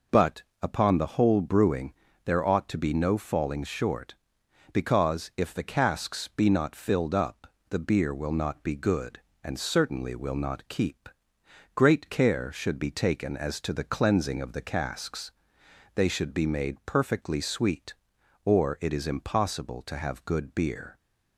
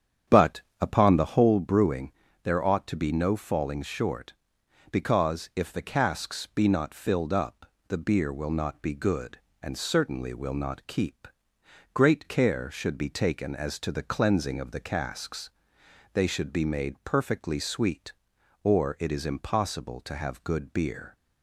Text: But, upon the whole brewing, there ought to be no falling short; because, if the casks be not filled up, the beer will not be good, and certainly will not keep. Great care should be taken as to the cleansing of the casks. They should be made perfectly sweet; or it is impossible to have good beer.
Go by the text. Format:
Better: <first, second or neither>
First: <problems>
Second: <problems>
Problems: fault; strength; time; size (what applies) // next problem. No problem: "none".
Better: first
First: none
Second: starts louder than the rest; strong; until 1.6 s; 9 dB